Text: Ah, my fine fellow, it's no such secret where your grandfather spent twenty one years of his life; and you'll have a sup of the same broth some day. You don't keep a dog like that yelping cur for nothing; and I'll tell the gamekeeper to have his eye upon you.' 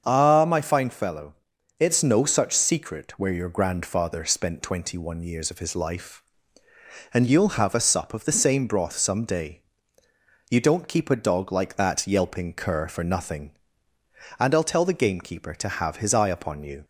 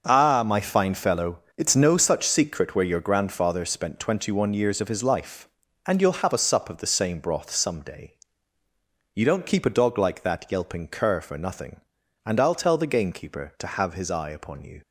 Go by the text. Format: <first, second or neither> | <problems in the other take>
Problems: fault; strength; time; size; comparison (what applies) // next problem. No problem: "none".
neither | starts louder than the rest; the same in both